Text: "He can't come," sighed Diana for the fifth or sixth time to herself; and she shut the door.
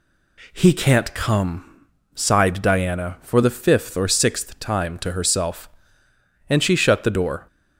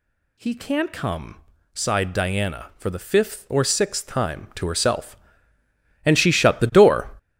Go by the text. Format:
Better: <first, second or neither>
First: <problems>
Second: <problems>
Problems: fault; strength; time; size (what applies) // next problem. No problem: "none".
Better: first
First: none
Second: gets louder; strong; throughout; 10.5 dB